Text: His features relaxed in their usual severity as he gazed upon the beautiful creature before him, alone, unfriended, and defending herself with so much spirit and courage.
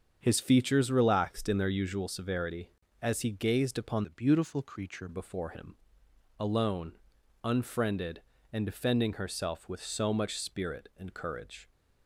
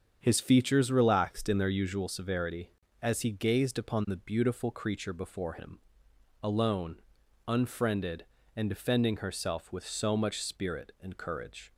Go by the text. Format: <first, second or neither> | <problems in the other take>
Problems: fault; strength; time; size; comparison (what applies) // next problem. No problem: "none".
second | starts louder than the rest; strong; until 1.2 s; 7 dB; strong in the second // changes voice from "the" to "creature"; from 4.0 to 5.0 s; 1.0 s long